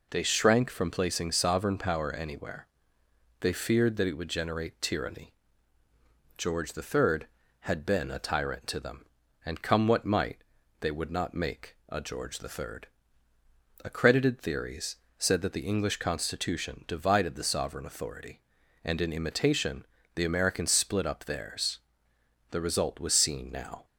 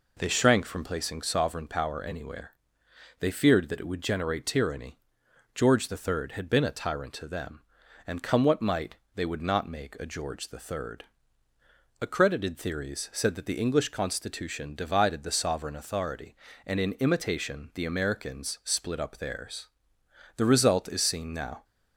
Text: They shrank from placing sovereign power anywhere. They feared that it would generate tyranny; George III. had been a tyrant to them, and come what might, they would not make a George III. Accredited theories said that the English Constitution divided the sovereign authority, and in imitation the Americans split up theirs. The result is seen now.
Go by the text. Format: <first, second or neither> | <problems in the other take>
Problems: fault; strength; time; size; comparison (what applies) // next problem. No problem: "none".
second | pauses between "theories" and "said"; slight; at 14.9 s; 0.20 s long // pauses between "imitation" and "the"; slight; at 19.8 s; 0.28 s long // says "was" for "is"; at 22.9 s